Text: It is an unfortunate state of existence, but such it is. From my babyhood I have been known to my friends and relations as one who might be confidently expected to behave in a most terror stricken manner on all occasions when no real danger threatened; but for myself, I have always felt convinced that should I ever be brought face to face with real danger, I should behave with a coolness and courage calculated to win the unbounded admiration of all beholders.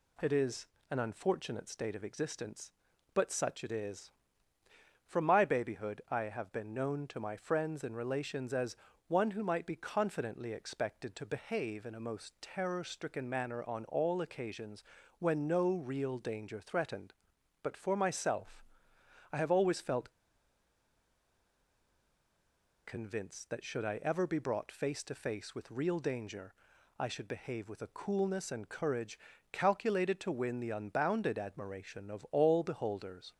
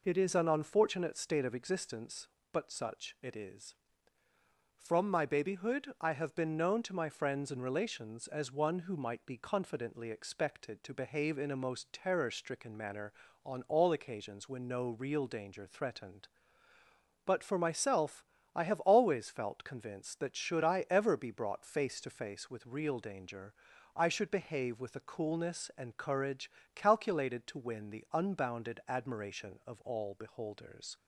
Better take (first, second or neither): second